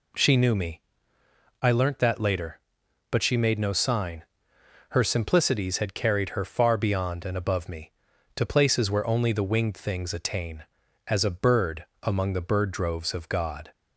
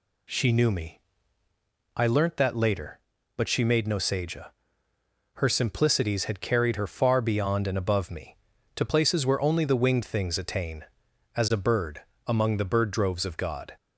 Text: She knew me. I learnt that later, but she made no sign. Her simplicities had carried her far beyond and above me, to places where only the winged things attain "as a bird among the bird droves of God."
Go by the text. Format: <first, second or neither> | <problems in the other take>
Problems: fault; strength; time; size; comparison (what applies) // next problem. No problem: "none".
first | says "seja" for "sign"; at 3.9 s // pauses between "bird" and "among"; slight; at 12.0 s; 0.26 s long; slight in the first